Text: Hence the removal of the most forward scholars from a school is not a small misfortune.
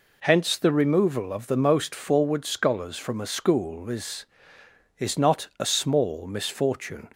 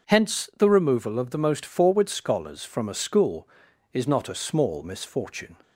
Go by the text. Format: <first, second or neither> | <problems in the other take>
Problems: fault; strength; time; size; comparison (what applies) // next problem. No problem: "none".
second | says "is" twice; at 4.9 s